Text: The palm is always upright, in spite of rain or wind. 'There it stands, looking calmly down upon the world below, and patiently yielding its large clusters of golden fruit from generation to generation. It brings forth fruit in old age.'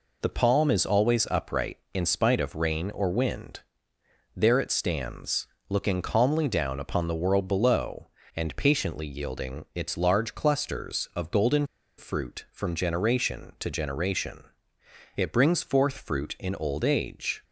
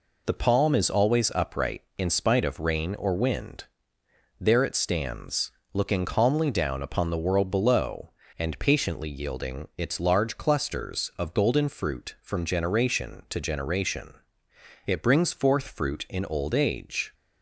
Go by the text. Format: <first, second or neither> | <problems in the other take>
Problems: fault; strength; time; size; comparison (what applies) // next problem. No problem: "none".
second | pauses between "golden" and "fruit"; slight; at 11.6 s; 0.31 s long